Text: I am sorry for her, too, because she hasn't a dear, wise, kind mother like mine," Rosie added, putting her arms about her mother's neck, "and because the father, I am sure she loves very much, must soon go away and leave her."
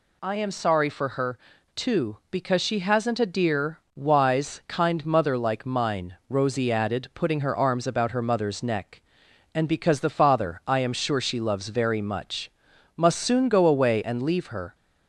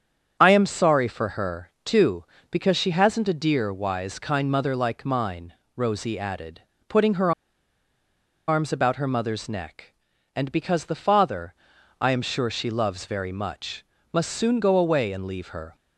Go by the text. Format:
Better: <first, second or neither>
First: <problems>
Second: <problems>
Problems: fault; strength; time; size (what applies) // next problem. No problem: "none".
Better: first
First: none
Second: starts louder than the rest; strong; until 1.4 s; 7.5 dB // pauses between "her" and "arms"; at 7.3 s; 1.1 s long